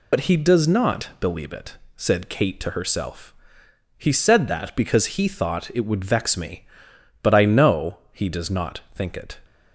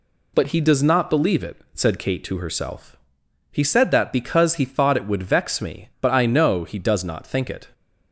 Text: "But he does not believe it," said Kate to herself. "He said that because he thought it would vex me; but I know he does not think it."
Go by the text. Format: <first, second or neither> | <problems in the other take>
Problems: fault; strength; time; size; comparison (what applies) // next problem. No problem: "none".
second | loses the start of "But"; at 0.1 s; 75 ms